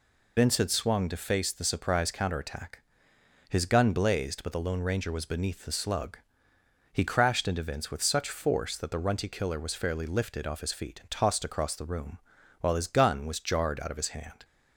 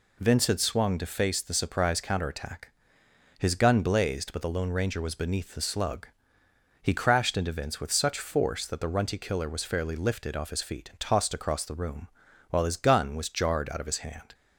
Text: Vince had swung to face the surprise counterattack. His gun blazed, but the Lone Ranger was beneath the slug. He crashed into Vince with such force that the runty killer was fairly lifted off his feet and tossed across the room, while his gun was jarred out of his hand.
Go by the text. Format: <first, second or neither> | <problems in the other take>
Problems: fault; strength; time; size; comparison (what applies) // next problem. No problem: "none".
second | loses the start of "Vince"; at 0.3 s; 70 ms